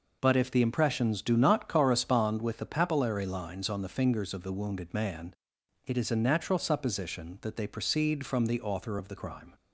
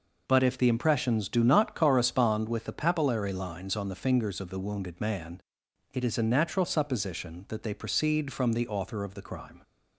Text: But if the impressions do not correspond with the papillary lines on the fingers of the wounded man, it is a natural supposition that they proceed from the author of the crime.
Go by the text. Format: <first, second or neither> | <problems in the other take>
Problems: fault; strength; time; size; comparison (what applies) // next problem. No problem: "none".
neither | none